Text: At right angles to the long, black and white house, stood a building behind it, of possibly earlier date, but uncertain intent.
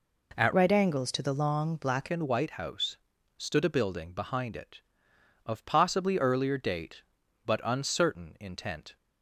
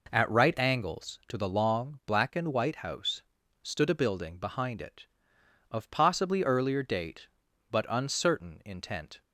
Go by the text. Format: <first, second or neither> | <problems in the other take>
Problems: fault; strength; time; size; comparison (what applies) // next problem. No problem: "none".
second | changes voice from "right" to "black"; from 0.5 to 2.0 s; 1.5 s long